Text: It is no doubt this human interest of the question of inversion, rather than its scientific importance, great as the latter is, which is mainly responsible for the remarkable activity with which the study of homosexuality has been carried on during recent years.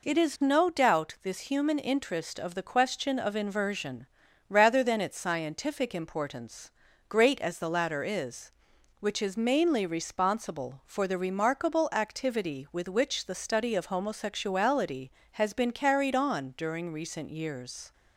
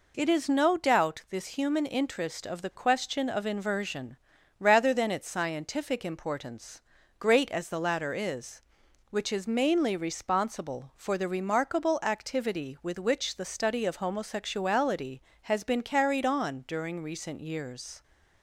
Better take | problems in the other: neither | none

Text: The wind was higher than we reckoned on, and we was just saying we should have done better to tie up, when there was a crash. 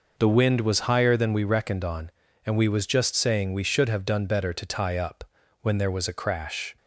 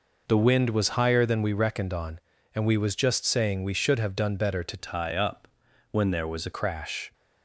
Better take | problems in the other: first | changes voice from "tie" to "a"; from 4.7 to 6.5 s; 1.8 s long

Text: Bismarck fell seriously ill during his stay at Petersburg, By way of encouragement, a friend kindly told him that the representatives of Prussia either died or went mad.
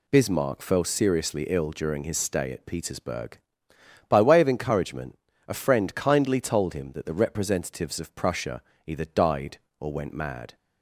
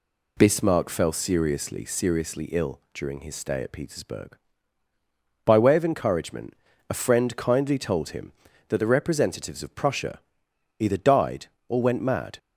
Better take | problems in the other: first | says "seriously" twice; at 1.8 s // pauses between "Prussia" and "either"; noticeable; at 10.1 s; 0.58 s long; slight in the first

